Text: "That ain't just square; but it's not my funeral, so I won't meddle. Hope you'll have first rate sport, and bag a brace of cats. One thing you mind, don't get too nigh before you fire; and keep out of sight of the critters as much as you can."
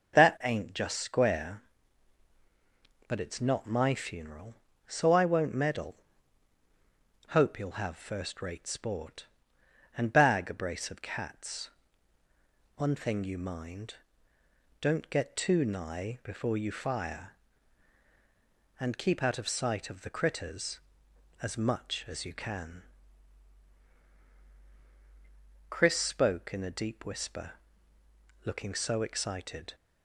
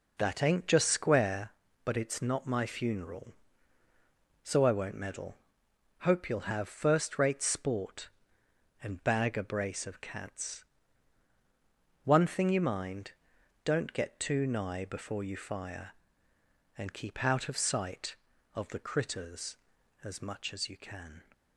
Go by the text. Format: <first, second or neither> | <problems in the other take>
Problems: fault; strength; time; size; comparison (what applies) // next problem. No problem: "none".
second | goes on to say "Chris spoke in a deep whisper looking so excited"; strong; from 25.6 s on; 4.0 s long